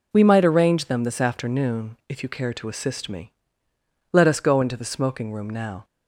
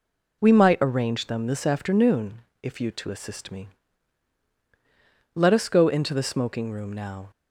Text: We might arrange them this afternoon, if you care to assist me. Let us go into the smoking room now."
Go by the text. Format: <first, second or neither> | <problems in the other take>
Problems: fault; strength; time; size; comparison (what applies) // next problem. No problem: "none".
first | skips "care"; at 2.9 s